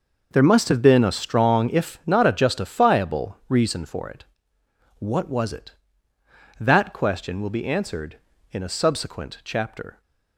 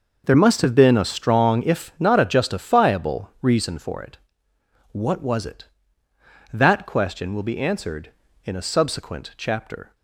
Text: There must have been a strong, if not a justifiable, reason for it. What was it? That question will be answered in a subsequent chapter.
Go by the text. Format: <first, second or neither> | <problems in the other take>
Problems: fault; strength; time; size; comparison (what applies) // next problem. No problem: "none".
neither | none